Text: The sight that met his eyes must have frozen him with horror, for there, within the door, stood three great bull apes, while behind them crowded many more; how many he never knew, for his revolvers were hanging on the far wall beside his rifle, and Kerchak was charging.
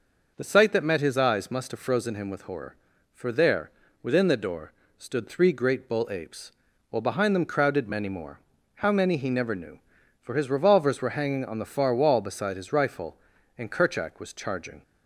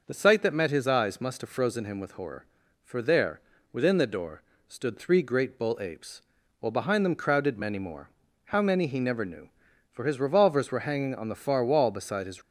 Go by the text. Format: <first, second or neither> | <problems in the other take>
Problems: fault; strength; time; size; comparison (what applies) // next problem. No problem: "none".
first | stops before "rifle and Kerchak was charging"; at 12.4 s